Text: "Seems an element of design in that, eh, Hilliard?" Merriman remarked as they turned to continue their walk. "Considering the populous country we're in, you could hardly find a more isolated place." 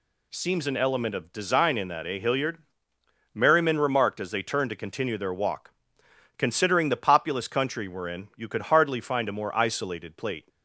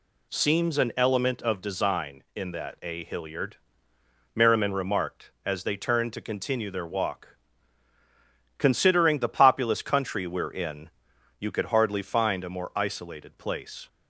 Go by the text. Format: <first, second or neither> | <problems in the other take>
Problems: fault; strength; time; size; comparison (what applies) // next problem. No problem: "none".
second | says "plate" for "place"; at 10.1 s